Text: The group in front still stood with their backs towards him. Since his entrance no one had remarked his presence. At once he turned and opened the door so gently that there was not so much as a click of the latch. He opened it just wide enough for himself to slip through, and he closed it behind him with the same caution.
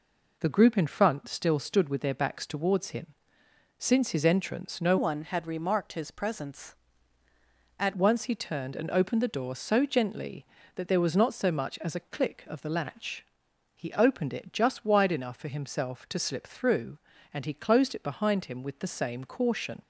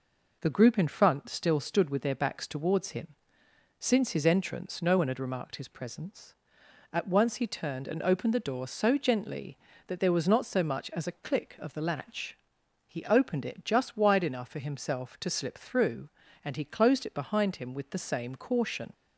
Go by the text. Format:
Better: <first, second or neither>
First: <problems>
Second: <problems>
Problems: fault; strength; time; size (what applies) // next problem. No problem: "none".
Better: second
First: changes voice from "one" to "At"; from 4.9 to 7.9 s; 3.0 s long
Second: none